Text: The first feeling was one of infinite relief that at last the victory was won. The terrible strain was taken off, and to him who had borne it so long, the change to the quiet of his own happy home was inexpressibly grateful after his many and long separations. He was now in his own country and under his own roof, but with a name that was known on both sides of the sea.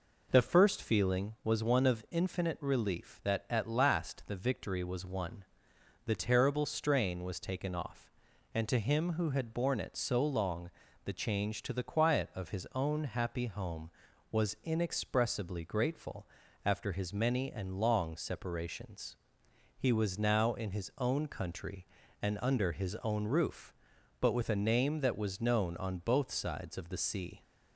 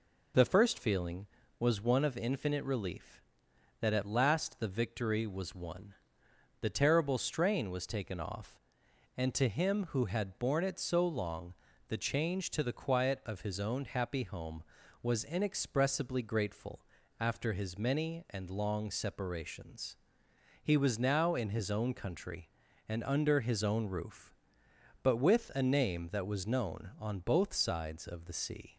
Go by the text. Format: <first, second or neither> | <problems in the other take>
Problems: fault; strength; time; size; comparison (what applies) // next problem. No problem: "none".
neither | pauses between "grateful" and "after"; slight; the same in both